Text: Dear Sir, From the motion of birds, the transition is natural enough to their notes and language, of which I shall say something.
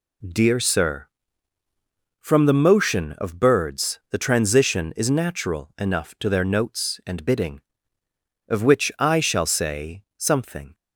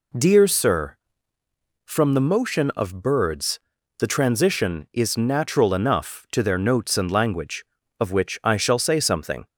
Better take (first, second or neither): second